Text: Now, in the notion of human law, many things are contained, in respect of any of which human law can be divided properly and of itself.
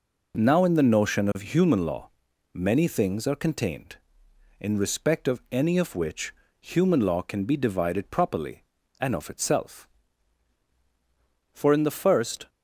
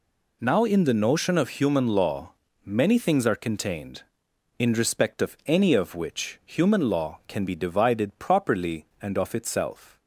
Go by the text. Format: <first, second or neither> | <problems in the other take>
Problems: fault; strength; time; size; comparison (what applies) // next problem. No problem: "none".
second | pauses between "which" and "human"; slight; at 6.3 s; 0.28 s long // goes on to say "For in the first"; noticeable; from 11.5 s on; 0.98 s long